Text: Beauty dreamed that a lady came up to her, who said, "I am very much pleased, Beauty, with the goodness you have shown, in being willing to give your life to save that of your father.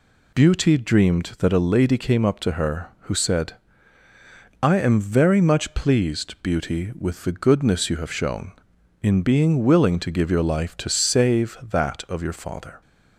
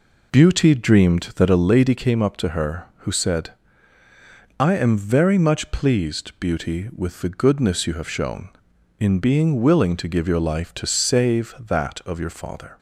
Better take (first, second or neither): first